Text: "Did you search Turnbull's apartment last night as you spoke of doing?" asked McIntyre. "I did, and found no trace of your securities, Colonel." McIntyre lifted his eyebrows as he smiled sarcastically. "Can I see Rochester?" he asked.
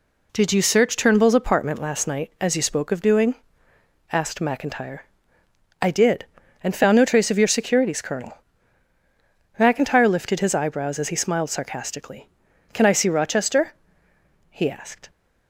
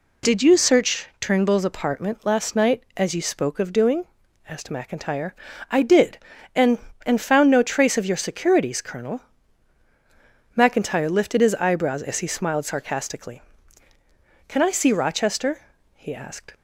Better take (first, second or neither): first